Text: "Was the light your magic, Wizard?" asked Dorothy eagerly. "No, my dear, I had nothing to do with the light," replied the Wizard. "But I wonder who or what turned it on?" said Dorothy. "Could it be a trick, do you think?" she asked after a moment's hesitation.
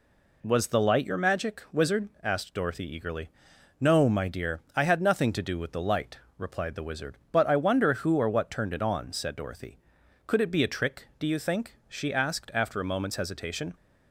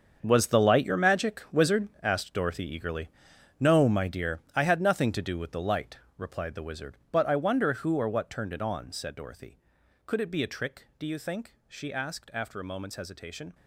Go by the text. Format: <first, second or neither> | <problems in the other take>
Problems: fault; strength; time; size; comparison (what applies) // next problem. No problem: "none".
first | gets quieter; strong; throughout; 12.5 dB